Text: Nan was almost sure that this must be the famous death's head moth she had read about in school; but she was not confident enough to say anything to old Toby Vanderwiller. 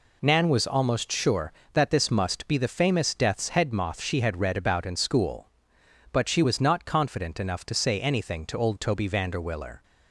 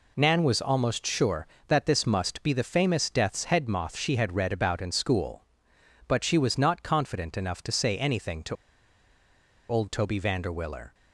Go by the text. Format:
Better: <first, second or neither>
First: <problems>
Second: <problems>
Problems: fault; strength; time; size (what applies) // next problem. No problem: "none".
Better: first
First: none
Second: pauses between "to" and "old"; at 8.5 s; 1.1 s long